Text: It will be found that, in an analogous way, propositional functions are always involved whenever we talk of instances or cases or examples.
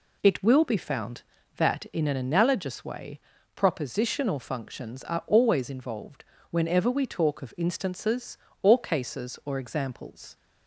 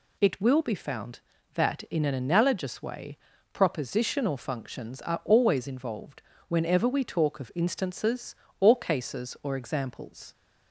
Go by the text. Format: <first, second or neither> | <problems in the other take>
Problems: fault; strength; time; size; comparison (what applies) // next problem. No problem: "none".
second | starts louder than the rest; slight; until 1.8 s; 2 dB // pauses between "involved" and "whenever"; slight; at 6.2 s; 0.24 s long; slight in the second